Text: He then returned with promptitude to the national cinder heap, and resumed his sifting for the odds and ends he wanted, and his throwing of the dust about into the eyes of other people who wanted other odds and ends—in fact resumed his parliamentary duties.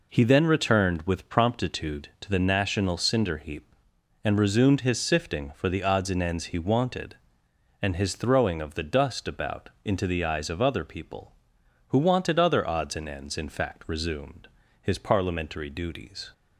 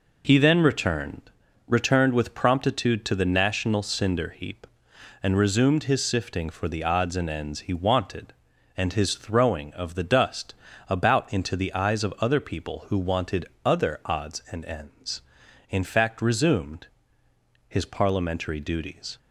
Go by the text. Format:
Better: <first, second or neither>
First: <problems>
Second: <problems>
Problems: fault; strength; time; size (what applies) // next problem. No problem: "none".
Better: first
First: pauses between "resumed" and "his"; slight; at 14.4 s; 0.34 s long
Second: says "returned" twice; at 1.6 s // pauses between "dust" and "about"; slight; at 10.5 s; 0.34 s long // pauses between "wanted" and "other"; slight; at 13.4 s; 0.16 s long // pauses between "resumed" and "his"; noticeable; at 16.8 s; 0.80 s long